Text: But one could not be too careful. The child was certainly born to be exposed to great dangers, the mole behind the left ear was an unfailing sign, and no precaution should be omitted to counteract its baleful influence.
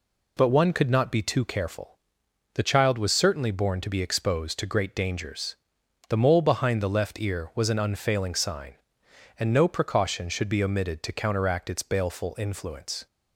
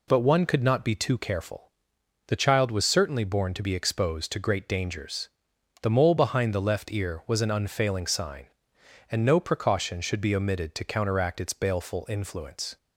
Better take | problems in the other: neither | none

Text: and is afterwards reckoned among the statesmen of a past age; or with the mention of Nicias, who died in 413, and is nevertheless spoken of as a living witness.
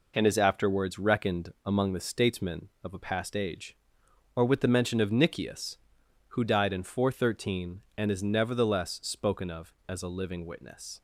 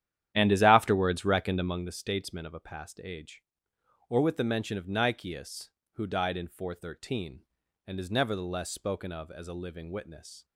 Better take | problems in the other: first | starts louder than the rest; strong; until 2.0 s; 11 dB

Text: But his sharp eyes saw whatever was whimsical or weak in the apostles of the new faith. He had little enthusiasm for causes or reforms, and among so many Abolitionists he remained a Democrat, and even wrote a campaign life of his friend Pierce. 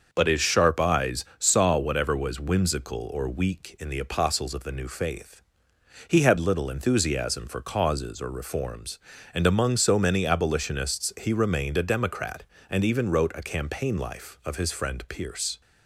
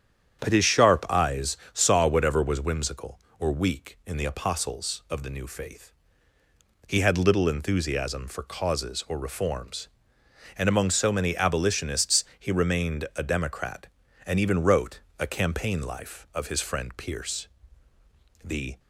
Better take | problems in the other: first | starts louder than the rest; strong; until 1.4 s; 9 dB; also in the first // pauses between "eyes" and "saw"; slight; at 1.5 s; 0.16 s long; slight in the first // pauses between "Abolitionists" and "he"; slight; at 12.2 s; 0.16 s long // pauses between "wrote" and "a"; slight; at 15.0 s; 0.18 s long // goes on to say "The"; slight; from 18.4 s on; 0.36 s long

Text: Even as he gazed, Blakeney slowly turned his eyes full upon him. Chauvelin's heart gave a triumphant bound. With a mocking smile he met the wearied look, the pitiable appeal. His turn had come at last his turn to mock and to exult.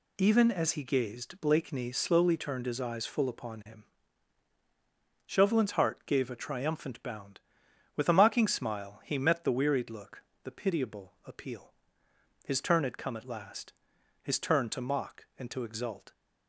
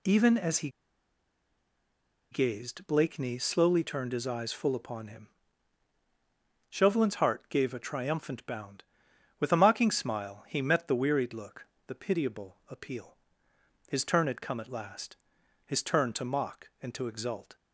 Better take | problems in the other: first | pauses between "he" and "gazed"; strong; at 0.6 s; 1.6 s long // pauses between "last" and "his"; noticeable; at 15.1 s; 0.50 s long; noticeable in the first

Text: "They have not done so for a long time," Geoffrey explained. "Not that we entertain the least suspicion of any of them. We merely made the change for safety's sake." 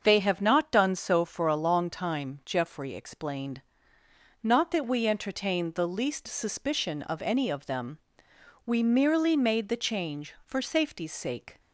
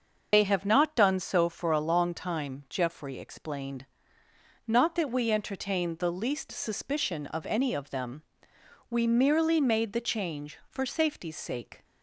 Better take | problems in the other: first | loses the start of "They"; at 0.3 s; 55 ms // starts louder than the rest; until 1.3 s; 6 dB; also in the first

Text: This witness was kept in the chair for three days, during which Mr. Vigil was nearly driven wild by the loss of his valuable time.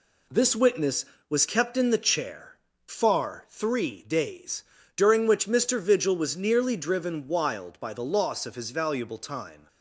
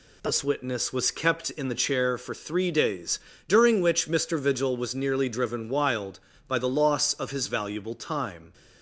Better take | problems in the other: second | says "far" for "for"; at 2.8 s

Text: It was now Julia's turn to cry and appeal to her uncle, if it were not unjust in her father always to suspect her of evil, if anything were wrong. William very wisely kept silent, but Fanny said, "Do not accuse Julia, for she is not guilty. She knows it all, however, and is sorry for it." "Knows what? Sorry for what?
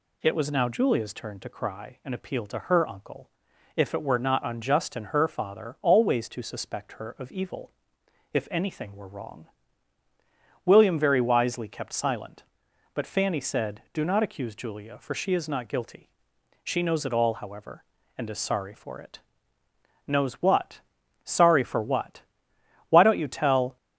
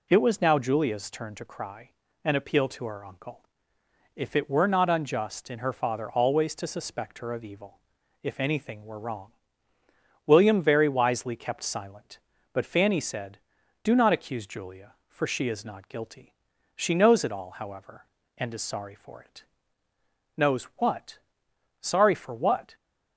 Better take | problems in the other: second | goes on to say "Why don't you tell"; noticeable; from 22.9 s on; 0.86 s long

